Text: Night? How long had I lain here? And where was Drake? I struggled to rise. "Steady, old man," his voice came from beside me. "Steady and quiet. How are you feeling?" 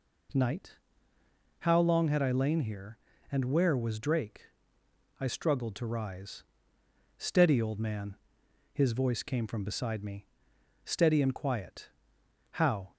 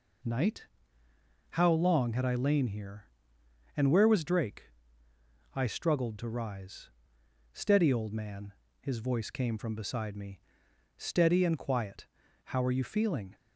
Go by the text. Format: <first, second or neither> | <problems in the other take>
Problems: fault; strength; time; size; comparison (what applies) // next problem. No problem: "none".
second | stops before "are you feeling"; at 12.9 s